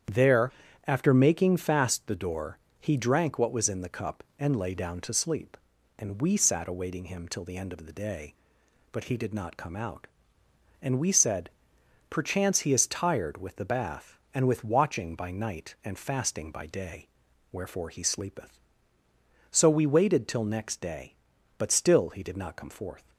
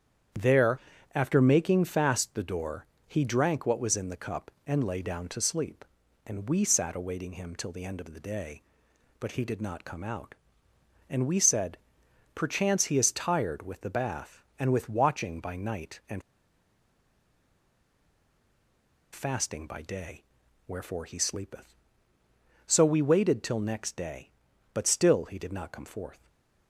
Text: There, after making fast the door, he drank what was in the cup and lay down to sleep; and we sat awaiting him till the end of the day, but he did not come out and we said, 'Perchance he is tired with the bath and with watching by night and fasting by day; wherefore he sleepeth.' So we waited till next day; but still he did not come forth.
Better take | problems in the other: first | starts louder than the rest; strong; until 1.6 s; 8.5 dB; strong in the first // pauses between "and" and "fasting"; strong; at 16.2 s; 2.9 s long // stays silent after the last word; slight; from 26.1 s on; 0.5 s long

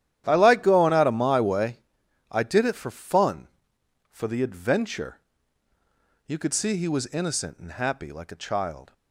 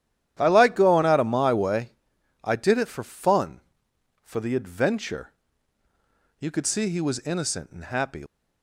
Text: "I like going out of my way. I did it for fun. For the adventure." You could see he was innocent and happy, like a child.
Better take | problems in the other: first | starts louder than the rest; strong; until 1.4 s; 11 dB; strong in the first // stops before "like a child"; at 8.2 s

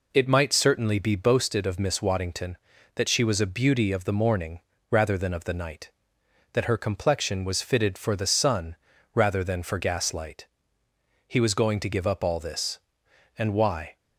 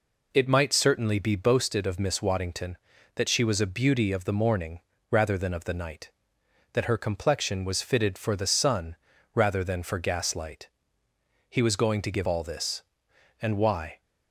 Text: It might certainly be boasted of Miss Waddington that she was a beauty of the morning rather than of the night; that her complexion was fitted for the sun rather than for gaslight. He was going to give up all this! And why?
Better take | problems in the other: first | pauses between "morning" and "rather"; slight; at 4.7 s; 0.32 s long; slight in the first // pauses between "sun" and "rather"; at 8.9 s; 0.40 s long; also in the first // skips "up"; at 12.2 s

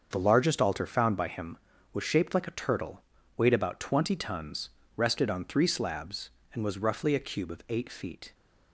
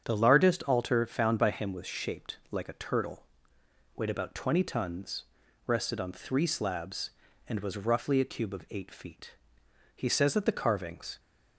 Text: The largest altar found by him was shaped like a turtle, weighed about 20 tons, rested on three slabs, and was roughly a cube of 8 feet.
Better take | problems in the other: first | starts louder than the rest; strong; until 1.0 s; 8 dB; also in the first // goes on to say "He says that the carvings"; noticeable; from 9.9 s on; 1.2 s long

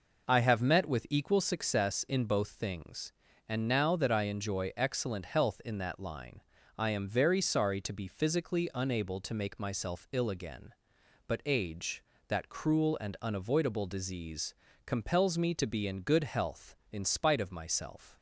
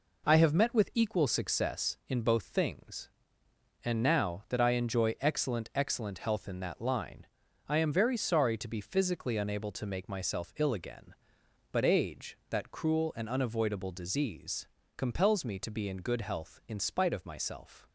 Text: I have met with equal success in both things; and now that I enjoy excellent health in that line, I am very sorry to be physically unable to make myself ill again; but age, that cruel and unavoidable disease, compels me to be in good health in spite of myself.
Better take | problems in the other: first | says "excellent" twice; at 5.7 s

